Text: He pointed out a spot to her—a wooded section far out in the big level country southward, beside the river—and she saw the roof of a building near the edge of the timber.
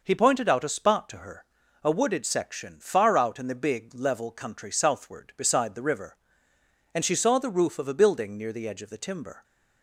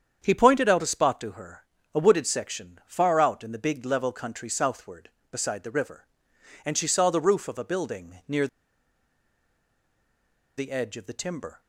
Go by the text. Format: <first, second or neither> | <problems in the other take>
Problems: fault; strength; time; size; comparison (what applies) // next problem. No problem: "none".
first | starts louder than the rest; strong; until 1.2 s; 8 dB // pauses between "near" and "the"; strong; at 8.4 s; 2.1 s long